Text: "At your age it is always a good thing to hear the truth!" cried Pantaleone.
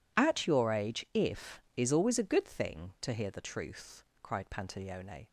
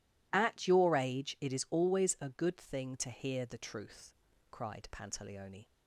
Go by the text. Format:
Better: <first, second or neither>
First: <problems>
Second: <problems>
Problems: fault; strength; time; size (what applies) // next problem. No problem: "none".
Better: second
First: says "if" for "it"; at 1.1 s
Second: none